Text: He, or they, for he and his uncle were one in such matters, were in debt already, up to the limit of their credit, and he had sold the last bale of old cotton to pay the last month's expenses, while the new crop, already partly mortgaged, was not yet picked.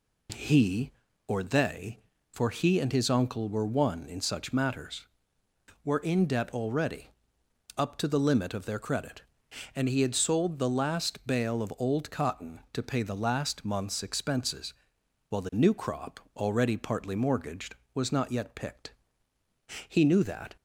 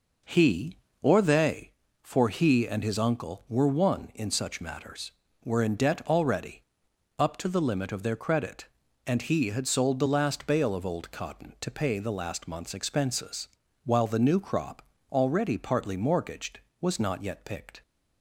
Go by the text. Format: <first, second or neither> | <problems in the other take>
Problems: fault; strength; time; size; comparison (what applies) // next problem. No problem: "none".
second | goes on to say "He knew that"; noticeable; from 19.8 s on; 0.68 s long